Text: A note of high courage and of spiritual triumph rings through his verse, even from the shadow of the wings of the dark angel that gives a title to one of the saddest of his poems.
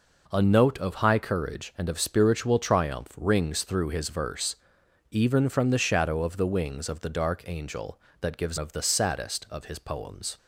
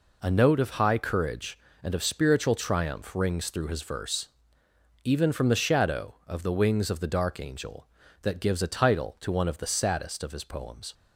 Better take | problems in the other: second | skips "a title to one"; at 8.5 s

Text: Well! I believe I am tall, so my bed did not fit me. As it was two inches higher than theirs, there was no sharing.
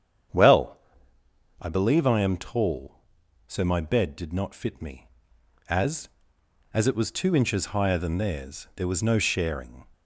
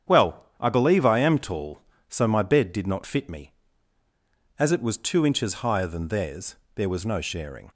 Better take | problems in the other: second | starts louder than the rest; strong; until 2.1 s; 8.5 dB; strong in the second // says "As" twice; at 6.7 s

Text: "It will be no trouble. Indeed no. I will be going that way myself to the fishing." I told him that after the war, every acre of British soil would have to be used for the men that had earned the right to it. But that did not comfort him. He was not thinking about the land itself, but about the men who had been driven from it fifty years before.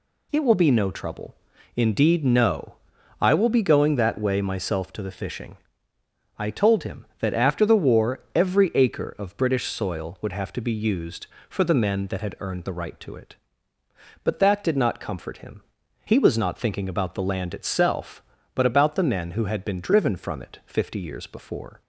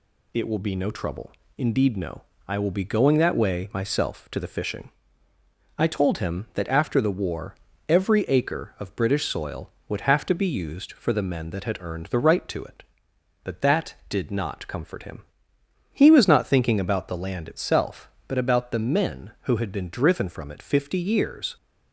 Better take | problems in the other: first | stops before "before"; at 21.5 s

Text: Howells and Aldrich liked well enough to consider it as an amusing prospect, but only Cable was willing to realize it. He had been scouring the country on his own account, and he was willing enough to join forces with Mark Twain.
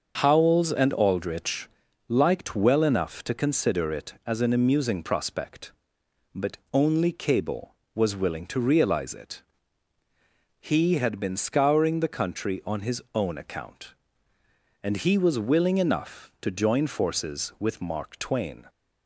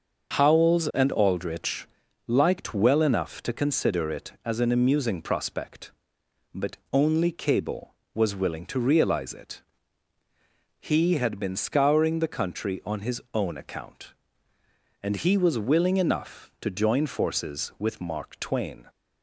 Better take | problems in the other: neither | starts louder than the rest; the same in both // pauses between "Aldrich" and "liked"; the same in both // pauses between "but" and "only"; slight; the same in both

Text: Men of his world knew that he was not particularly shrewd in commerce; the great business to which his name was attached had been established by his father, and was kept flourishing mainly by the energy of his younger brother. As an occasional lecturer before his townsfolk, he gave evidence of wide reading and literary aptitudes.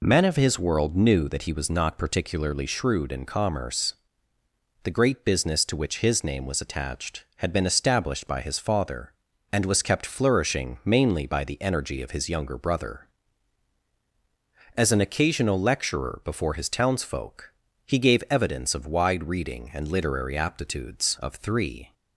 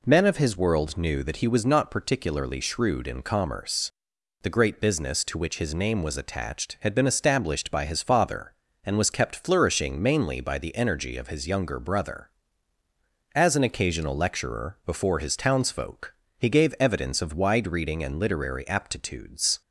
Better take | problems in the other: second | goes on to say "Of three"; noticeable; from 21.2 s on; 0.72 s long

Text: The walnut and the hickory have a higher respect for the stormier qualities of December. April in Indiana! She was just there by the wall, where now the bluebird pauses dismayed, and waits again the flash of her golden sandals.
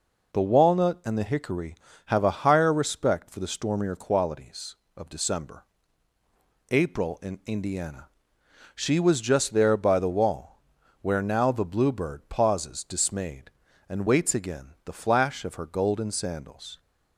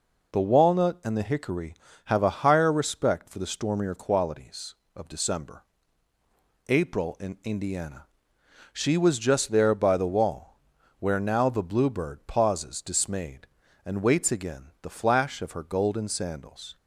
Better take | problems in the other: neither | pauses between "again" and "the"; slight; the same in both

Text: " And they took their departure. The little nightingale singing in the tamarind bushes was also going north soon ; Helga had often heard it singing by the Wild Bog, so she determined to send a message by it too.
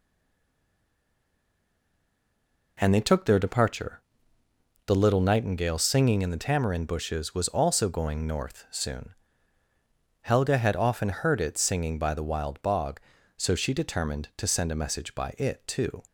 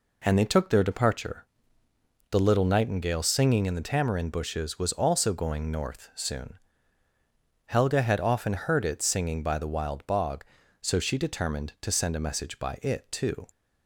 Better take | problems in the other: second | stays silent before the first word; strong; until 2.7 s; 2.7 s long

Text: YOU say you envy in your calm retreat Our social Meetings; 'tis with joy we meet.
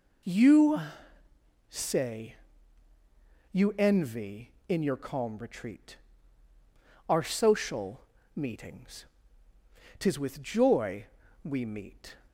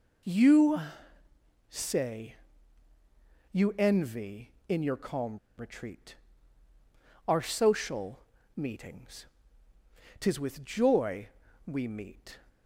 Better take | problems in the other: first | pauses between "YOU" and "say"; noticeable; at 0.7 s; 0.90 s long; noticeable in the first // pauses between "say" and "you"; at 2.3 s; 1.1 s long; also in the first // pauses between "calm" and "retreat"; slight; at 5.3 s; 0.20 s long // pauses between "retreat" and "Our"; at 6.1 s; 1.1 s long; also in the first // pauses between "social" and "Meetings"; at 8.1 s; 0.38 s long; slight in the first // pauses between "joy" and "we"; at 11.2 s; 0.38 s long; also in the first

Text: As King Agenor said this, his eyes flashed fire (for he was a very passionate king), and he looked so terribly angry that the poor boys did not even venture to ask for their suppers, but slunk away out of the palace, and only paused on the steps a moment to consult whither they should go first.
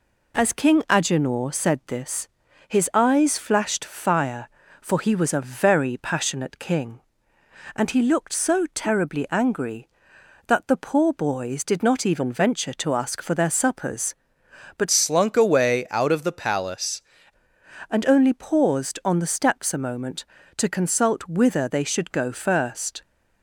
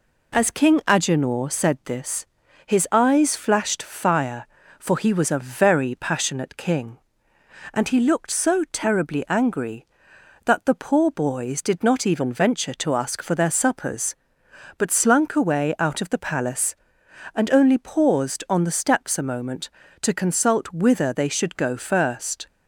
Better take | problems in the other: second | changes voice from "slunk" to "palace"; from 14.9 to 17.0 s; 2.1 s long

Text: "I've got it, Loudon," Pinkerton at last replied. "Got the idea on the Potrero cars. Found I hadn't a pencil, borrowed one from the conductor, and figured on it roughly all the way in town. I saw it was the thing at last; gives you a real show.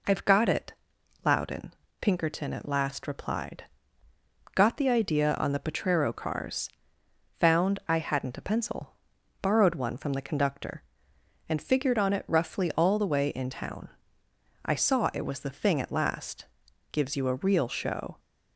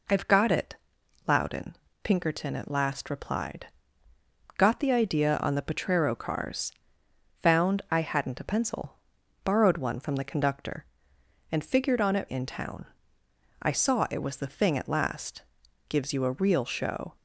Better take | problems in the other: first | skips "roughly all the way"; at 12.2 s

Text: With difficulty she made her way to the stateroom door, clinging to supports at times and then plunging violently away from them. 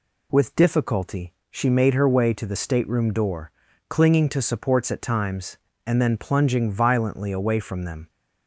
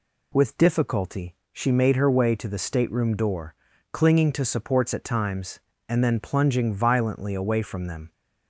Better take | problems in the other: neither | pauses between "difficulty" and "she"; slight; the same in both

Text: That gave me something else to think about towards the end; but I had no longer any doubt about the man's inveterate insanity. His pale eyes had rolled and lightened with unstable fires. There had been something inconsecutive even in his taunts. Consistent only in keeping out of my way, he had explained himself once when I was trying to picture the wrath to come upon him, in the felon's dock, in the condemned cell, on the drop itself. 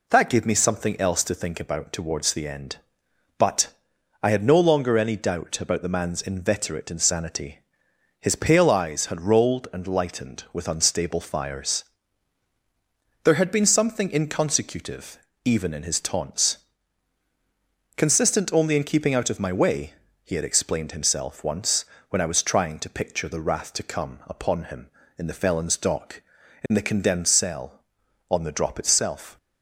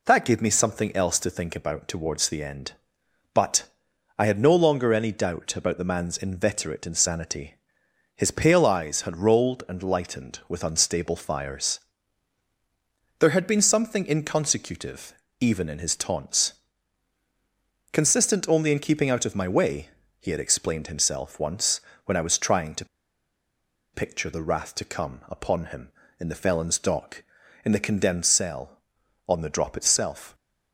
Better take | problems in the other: first | pauses between "but" and "I"; noticeable; at 3.6 s; 0.50 s long; noticeable in the first // pauses between "inconsecutive" and "even"; slight; at 15.1 s; 0.24 s long; slight in the first // pauses between "once" and "when"; slight; at 21.8 s; 0.24 s long; slight in the first // pauses between "to" and "picture"; at 22.8 s; 1.0 s long

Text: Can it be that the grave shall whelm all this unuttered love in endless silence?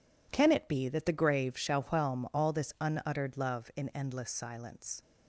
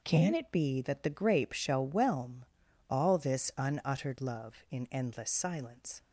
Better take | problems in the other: first | says "grape" for "grave"; at 1.0 s // pauses between "whelm" and "all"; noticeable; at 2.4 s; 0.46 s long

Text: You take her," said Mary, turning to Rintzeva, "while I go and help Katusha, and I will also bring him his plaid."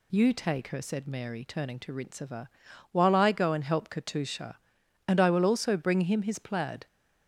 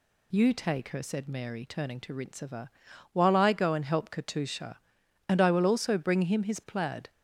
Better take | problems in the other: neither | none

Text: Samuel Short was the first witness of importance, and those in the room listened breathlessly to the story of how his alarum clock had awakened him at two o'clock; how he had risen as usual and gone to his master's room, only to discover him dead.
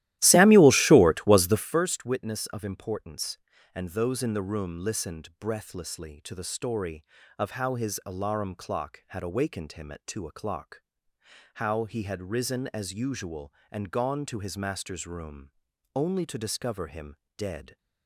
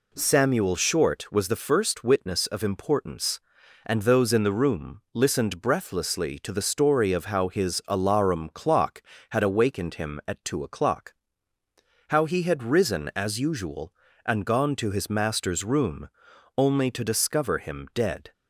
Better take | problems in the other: second | starts louder than the rest; strong; until 1.8 s; 15 dB // pauses between "him" and "dead"; slight; at 17.1 s; 0.22 s long

